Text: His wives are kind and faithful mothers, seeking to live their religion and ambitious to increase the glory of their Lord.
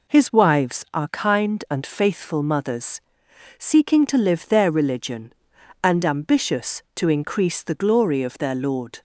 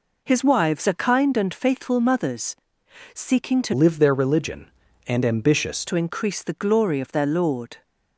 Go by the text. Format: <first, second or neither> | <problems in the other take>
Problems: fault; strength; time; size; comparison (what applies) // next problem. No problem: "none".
first | changes voice from "live" to "ambitious"; from 3.7 to 5.8 s; 2.1 s long